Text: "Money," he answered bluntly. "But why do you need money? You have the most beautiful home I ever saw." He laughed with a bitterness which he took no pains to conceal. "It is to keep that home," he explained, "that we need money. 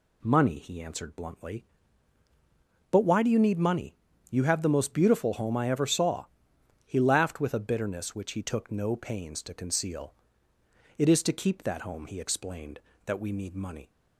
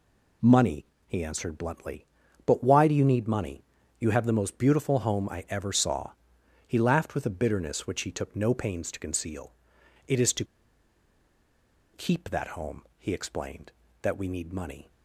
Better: first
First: none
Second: pauses between "to" and "keep"; strong; at 10.4 s; 1.4 s long

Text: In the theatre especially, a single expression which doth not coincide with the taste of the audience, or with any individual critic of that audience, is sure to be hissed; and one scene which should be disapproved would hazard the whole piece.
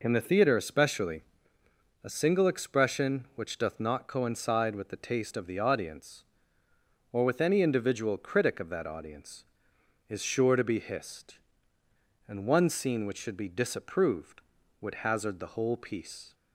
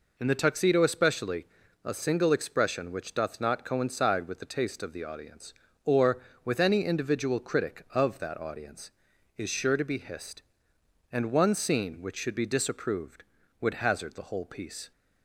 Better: first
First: none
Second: says "tuxedo" for "theatre"; at 0.3 s

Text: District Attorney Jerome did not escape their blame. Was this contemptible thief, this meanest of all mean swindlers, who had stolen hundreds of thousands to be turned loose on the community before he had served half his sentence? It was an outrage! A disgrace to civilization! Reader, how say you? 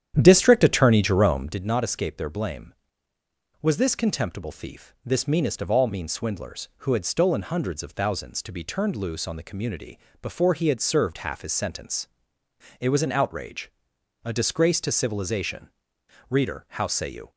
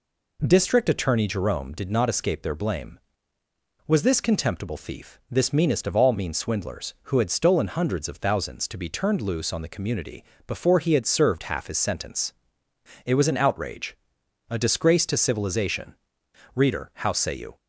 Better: second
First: starts louder than the rest; strong; until 1.7 s; 10 dB // pauses between "community" and "before"; slight; at 9.9 s; 0.22 s long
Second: pauses between "community" and "before"; slight; at 10.2 s; 0.22 s long

